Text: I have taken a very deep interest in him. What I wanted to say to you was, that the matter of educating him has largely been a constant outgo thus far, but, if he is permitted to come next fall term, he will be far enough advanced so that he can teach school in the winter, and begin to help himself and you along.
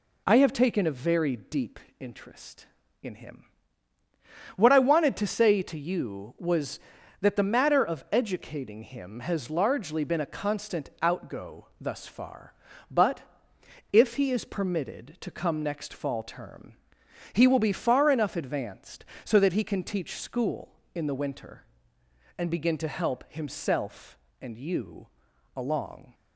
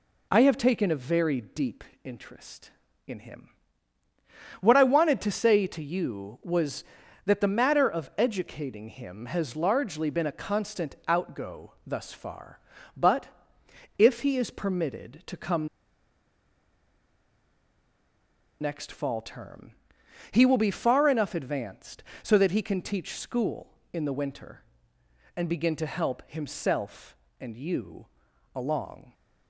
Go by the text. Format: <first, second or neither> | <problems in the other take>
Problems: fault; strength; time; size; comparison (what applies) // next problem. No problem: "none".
first | pauses between "deep" and "interest"; slight; at 1.8 s; 0.18 s long; slight in the first // pauses between "come" and "next"; strong; at 15.6 s; 2.9 s long // pauses between "you" and "along"; noticeable; at 28.0 s; 0.48 s long; noticeable in the first